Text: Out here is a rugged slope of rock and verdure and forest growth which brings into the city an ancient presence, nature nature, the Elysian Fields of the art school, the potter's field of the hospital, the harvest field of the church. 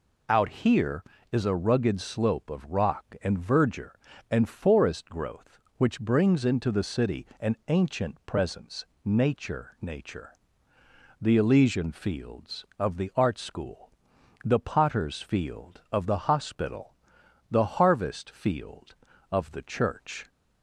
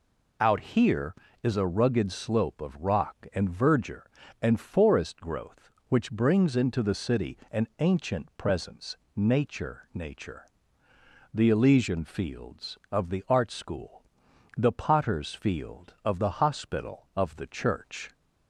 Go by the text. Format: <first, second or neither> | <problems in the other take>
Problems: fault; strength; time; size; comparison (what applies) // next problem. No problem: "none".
first | pauses between "city" and "an"; slight; at 7.3 s; 0.16 s long; slight in the first // skips "the harvest field"; at 17.1 s